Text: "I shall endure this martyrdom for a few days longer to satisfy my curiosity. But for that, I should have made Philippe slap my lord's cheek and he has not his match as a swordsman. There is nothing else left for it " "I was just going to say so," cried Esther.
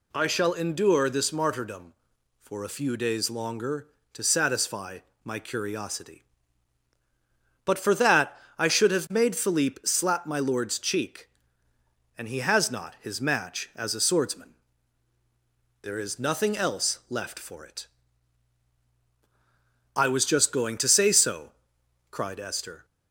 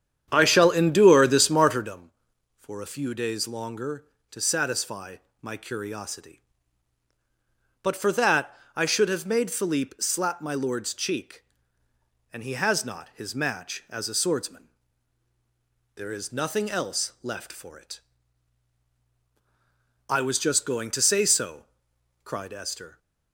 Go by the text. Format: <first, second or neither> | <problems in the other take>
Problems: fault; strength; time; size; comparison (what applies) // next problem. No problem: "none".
first | starts louder than the rest; strong; until 2.0 s; 9 dB // pauses between "satisfy" and "my"; slight; at 5.1 s; 0.24 s long; slight in the first